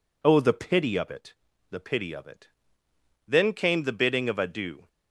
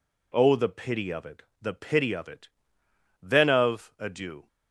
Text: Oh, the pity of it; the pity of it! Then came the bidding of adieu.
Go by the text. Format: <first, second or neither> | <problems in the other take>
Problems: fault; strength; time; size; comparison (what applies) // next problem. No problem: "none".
first | skips "came the bidding"; at 3.5 s